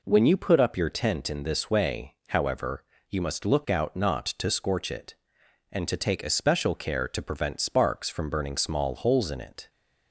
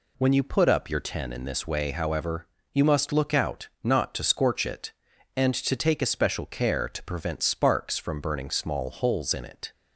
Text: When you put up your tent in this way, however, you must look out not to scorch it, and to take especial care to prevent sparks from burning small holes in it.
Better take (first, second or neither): first